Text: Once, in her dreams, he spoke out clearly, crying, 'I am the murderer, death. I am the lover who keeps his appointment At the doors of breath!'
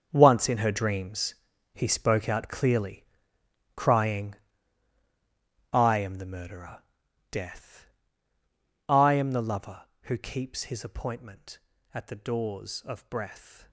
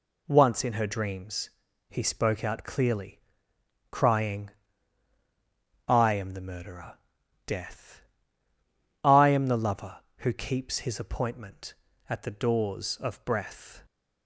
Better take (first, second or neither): second